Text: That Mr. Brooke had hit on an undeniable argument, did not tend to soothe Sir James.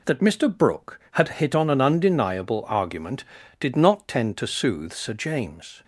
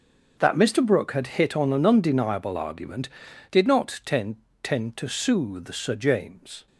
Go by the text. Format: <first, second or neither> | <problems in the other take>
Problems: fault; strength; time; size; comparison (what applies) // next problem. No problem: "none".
first | starts louder than the rest; until 1.3 s; 6 dB // says "tend" twice; at 4.6 s